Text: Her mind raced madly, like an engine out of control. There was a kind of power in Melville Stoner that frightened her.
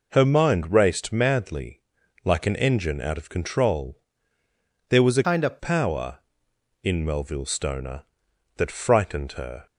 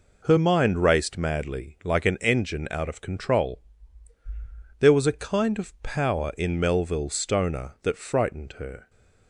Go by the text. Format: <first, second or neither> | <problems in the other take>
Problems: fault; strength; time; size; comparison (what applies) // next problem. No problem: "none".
second | changes voice from "kind" to "of"; from 5.2 to 5.5 s; 0.3 s long